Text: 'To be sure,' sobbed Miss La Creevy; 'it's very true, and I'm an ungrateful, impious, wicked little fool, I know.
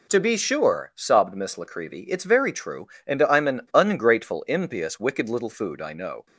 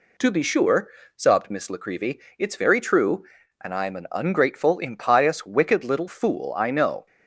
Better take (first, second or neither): second